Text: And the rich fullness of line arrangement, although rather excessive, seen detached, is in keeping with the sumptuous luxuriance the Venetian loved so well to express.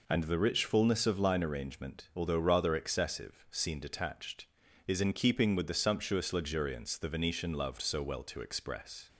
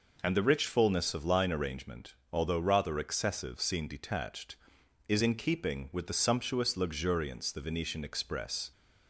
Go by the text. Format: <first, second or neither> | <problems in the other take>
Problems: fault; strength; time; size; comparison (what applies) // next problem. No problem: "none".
first | skips "loved so well to"; at 8.0 s